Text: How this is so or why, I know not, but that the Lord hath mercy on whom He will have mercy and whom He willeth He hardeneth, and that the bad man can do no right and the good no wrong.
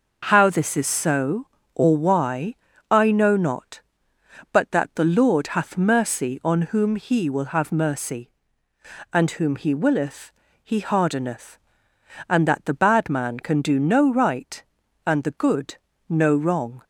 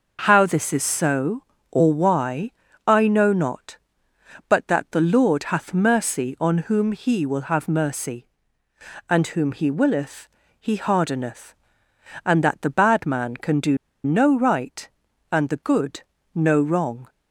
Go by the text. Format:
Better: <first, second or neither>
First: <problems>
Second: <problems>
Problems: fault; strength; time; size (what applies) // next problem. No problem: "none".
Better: first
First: pauses between "willeth" and "He"; slight; at 10.3 s; 0.32 s long // pauses between "good" and "no"; slight; at 15.7 s; 0.30 s long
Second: pauses between "willeth" and "He"; slight; at 10.2 s; 0.32 s long // pauses between "do" and "no"; slight; at 13.7 s; 0.27 s long // pauses between "good" and "no"; slight; at 16.0 s; 0.30 s long